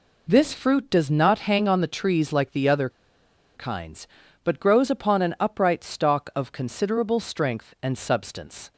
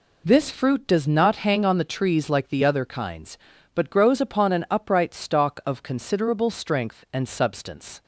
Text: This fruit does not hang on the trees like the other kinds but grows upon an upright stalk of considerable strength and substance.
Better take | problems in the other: second | pauses between "other" and "kinds"; noticeable; at 2.8 s; 0.66 s long

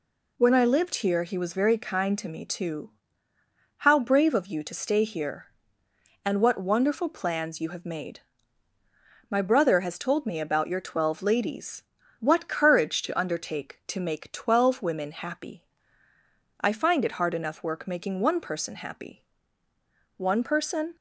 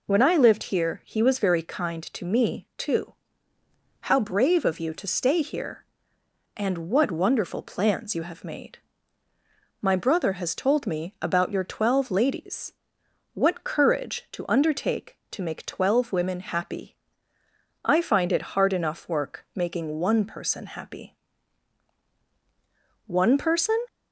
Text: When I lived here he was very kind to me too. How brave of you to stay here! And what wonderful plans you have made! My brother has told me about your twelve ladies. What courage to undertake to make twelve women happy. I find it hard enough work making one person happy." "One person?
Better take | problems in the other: neither | none

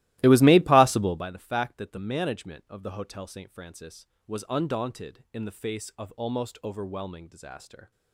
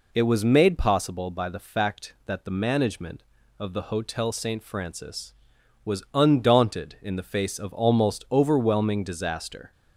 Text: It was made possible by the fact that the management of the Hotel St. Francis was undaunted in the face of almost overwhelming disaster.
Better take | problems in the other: second | starts louder than the rest; strong; until 1.2 s; 16.5 dB

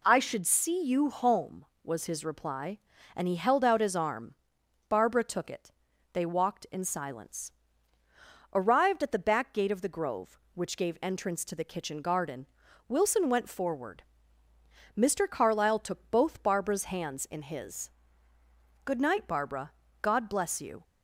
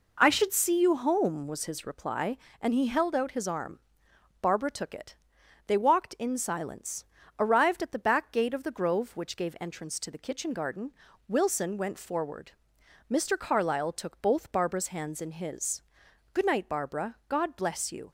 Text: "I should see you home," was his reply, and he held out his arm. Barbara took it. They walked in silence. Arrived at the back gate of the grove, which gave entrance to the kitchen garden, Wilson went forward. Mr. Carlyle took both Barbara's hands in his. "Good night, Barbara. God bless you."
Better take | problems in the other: neither | none

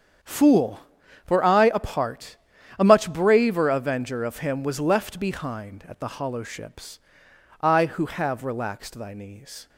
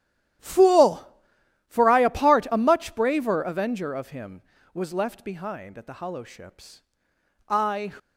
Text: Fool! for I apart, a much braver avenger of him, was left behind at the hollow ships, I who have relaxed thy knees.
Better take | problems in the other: first | starts louder than the rest; strong; until 1.8 s; 11 dB; strong in the first // stops before "who have relaxed thy knees"; at 7.9 s

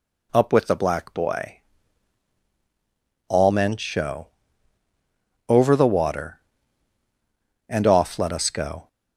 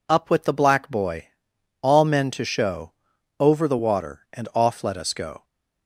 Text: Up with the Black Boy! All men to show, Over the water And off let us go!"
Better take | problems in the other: second | skips "to"; at 3.7 s

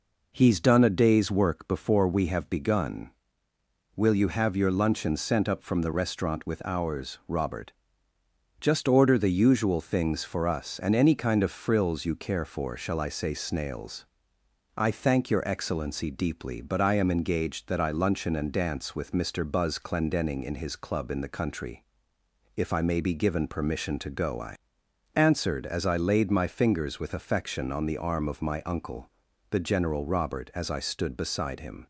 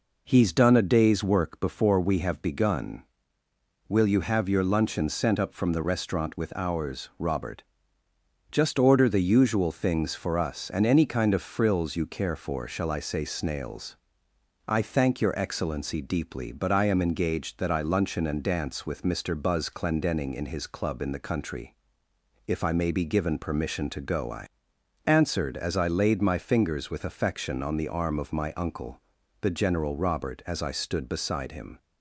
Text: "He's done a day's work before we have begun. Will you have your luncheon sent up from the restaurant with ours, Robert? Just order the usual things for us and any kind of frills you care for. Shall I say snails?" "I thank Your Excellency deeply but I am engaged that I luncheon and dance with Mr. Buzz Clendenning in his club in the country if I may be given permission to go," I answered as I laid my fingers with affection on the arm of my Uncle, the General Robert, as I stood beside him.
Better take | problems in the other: neither | pauses between "country" and "if"; noticeable; the same in both // pauses between "I" and "answered"; noticeable; the same in both

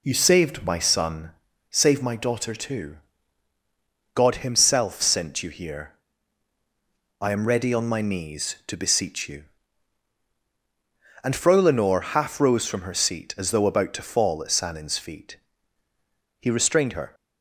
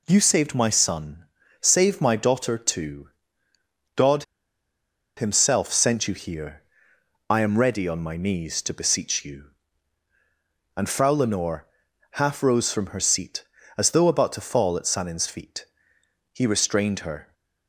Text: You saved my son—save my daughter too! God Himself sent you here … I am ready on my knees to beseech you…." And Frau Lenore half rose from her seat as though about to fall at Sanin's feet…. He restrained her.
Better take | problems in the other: first | pauses between "God" and "Himself"; noticeable; at 4.2 s; 0.93 s long // pauses between "Lenore" and "half"; noticeable; at 11.6 s; 0.46 s long

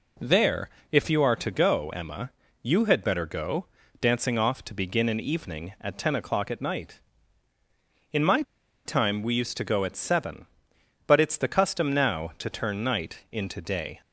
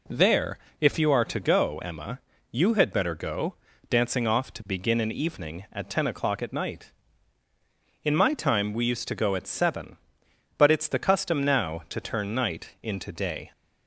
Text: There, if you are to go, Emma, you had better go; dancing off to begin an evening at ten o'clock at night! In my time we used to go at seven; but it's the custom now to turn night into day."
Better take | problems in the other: second | pauses between "my" and "time"; at 8.4 s; 0.43 s long

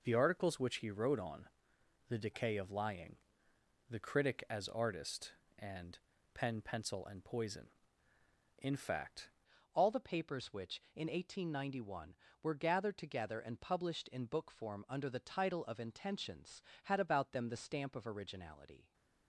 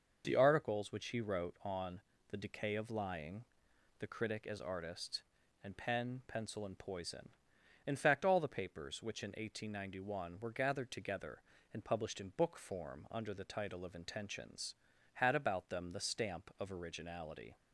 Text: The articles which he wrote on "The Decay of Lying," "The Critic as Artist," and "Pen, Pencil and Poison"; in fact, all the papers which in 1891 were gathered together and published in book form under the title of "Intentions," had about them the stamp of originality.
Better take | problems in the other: second | pauses between "on" and "The"; noticeable; at 1.4 s; 0.62 s long; slight in the second // pauses between "and" and "Pen"; slight; at 5.9 s; 0.34 s long // changes voice at "all"; from 9.7 s on; 9.2 s long

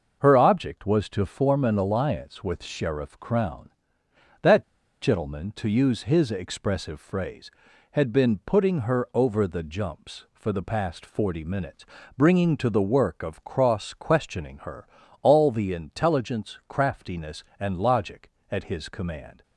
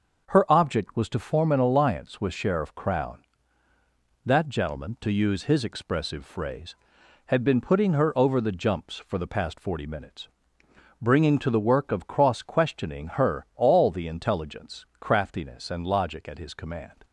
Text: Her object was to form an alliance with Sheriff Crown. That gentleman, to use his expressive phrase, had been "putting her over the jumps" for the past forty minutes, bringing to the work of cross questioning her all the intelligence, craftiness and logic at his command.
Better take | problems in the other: second | pauses between "That" and "gentleman"; at 4.6 s; 0.38 s long // pauses between "her" and "all"; slight; at 14.8 s; 0.36 s long

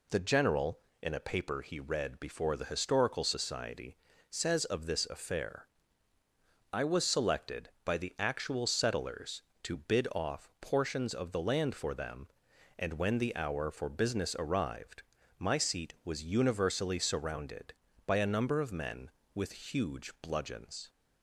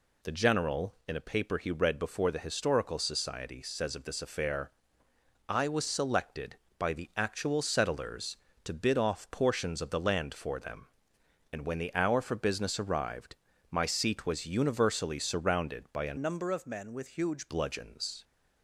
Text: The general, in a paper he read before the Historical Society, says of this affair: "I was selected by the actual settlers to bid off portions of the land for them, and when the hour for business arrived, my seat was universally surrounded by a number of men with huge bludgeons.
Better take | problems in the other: first | changes voice from "number" to "huge"; from 16.1 to 17.4 s; 1.3 s long

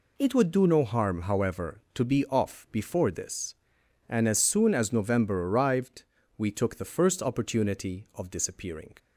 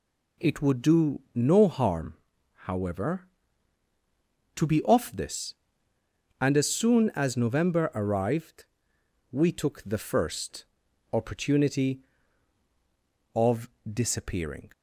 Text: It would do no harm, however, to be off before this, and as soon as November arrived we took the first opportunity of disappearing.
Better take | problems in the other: first | skips "before"; at 5.1 s // pauses between "arrived" and "we"; noticeable; at 8.6 s; 0.66 s long; slight in the first // pauses between "first" and "opportunity"; noticeable; at 10.6 s; 0.48 s long // pauses between "of" and "disappearing"; slight; at 13.6 s; 0.24 s long

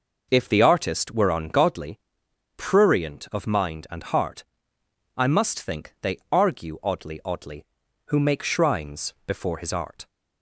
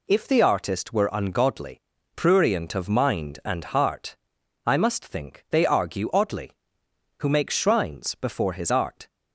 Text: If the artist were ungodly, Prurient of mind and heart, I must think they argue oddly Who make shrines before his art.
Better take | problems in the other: second | says "oddly" twice; at 7.2 s

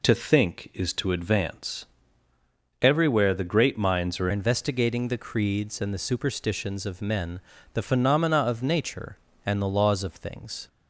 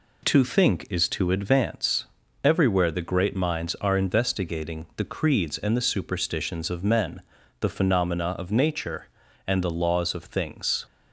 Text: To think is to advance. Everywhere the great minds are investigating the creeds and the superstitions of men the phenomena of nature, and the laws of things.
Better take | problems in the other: second | changes voice at "investigating"; from 4.3 s on; 6.3 s long // pauses between "men" and "the"; slight; at 7.3 s; 0.34 s long; also in the second

